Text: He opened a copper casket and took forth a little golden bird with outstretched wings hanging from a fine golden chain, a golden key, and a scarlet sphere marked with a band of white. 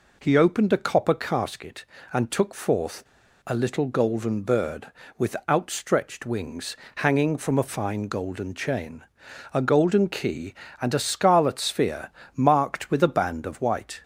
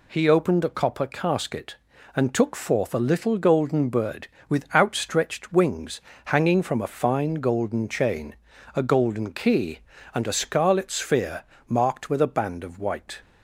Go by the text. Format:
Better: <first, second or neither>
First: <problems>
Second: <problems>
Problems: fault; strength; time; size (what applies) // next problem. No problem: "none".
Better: second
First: pauses between "forth" and "a"; at 3.0 s; 0.42 s long // pauses between "wings" and "hanging"; slight; at 6.7 s; 0.20 s long // pauses between "sphere" and "marked"; slight; at 12.1 s; 0.24 s long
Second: pauses between "wings" and "hanging"; slight; at 6.0 s; 0.24 s long // pauses between "sphere" and "marked"; slight; at 11.4 s; 0.24 s long